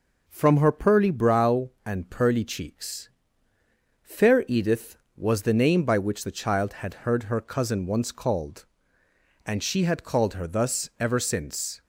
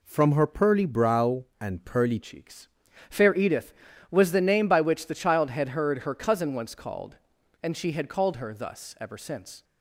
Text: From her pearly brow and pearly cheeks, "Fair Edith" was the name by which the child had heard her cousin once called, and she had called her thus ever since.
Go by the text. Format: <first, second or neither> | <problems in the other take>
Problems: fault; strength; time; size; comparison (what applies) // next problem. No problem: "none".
first | changes voice at "cheeks"; from 2.2 s on; 7.4 s long